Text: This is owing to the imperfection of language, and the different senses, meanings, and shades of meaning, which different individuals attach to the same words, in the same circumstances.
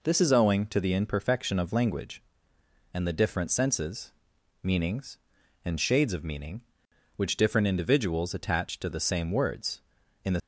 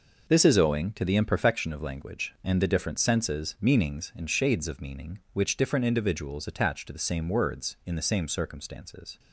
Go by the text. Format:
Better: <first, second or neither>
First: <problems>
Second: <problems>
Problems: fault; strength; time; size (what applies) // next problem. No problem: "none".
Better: second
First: stops before "same circumstances"; at 10.3 s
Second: none